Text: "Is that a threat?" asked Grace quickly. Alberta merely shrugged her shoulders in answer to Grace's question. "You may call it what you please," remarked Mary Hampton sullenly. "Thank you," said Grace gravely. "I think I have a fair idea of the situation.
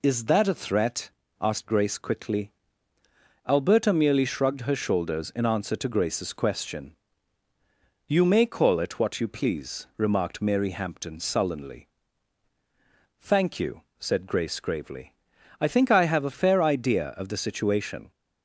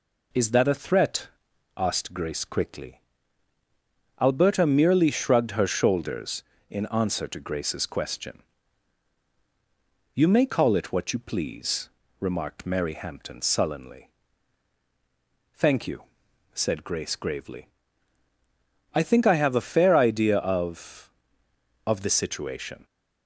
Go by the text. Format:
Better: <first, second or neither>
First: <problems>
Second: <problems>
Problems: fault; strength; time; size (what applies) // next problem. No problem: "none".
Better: first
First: none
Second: says "of" twice; at 21.8 s